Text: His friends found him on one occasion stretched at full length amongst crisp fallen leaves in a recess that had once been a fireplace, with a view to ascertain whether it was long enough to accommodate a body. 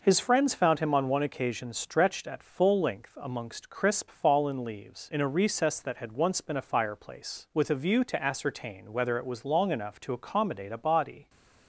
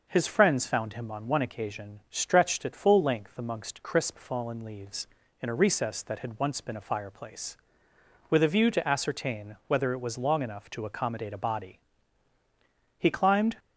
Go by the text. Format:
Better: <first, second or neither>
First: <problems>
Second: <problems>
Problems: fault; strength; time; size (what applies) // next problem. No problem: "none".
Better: first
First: none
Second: goes on to say "He climbed"; from 12.9 s on; 0.58 s long